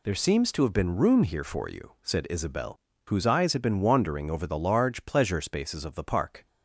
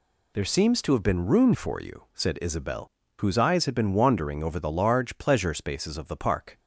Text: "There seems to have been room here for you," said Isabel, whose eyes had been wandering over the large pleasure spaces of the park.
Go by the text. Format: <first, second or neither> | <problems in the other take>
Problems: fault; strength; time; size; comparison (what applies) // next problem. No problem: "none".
first | skips "here"; at 1.5 s